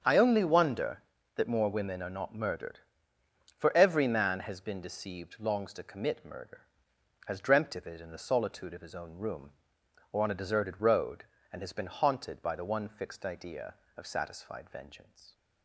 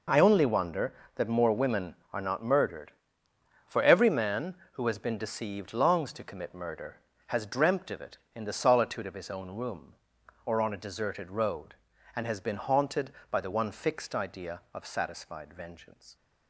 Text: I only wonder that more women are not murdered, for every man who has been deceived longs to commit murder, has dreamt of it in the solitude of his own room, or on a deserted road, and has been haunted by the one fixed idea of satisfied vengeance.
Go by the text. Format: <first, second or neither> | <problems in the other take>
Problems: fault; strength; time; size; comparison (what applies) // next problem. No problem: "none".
second | starts louder than the rest; strong; until 1.0 s; 7.5 dB // skips "who"; at 4.3 s